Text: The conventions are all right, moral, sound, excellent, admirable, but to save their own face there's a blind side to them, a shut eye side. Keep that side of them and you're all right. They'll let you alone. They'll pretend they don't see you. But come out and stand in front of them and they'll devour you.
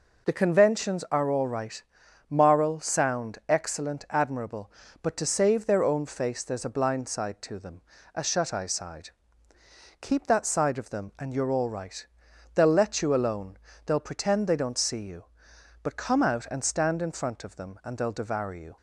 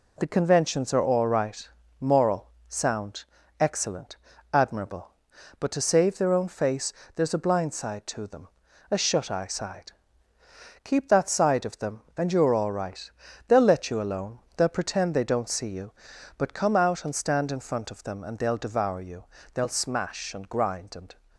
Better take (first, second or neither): first